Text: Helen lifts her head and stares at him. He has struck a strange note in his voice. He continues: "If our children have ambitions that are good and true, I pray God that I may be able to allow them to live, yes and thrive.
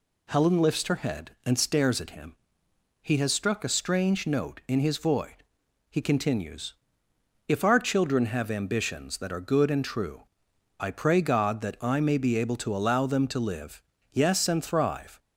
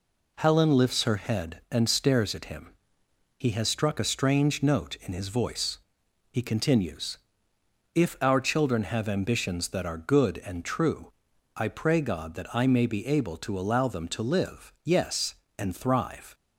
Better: second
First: says "void" for "voice"; at 4.9 s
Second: none

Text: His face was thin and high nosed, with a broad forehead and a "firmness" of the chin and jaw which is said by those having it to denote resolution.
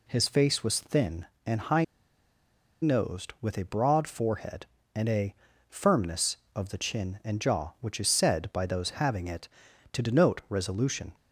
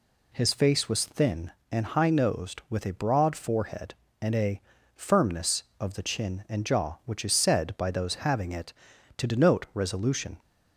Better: second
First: pauses between "high" and "nosed"; at 1.8 s; 0.98 s long // pauses between "a" and "firmness"; slight; at 5.3 s; 0.34 s long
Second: pauses between "a" and "firmness"; slight; at 4.6 s; 0.34 s long

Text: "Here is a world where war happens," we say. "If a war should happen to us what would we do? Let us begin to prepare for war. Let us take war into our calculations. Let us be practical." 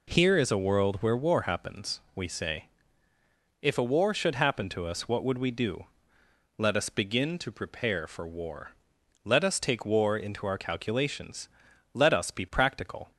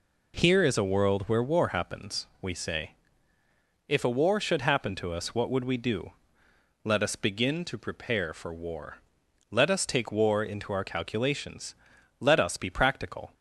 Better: neither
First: none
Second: none

